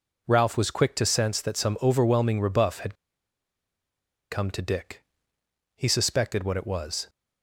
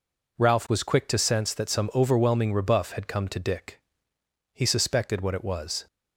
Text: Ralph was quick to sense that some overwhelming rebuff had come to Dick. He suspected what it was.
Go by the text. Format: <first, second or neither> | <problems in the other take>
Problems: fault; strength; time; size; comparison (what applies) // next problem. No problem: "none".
second | pauses between "had" and "come"; strong; at 2.9 s; 1.3 s long